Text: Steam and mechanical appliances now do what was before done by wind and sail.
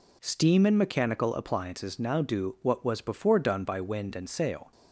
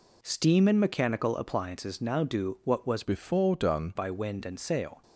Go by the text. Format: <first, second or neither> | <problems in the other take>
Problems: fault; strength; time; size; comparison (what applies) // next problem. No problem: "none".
first | changes voice from "before" to "done"; from 3.0 to 3.9 s; 0.9 s long